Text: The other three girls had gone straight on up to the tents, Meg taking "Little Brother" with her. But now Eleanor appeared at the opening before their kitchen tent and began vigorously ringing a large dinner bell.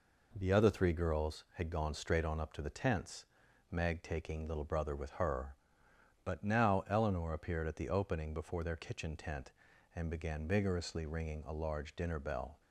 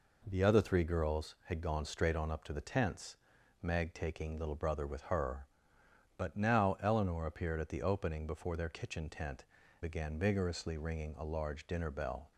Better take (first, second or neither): first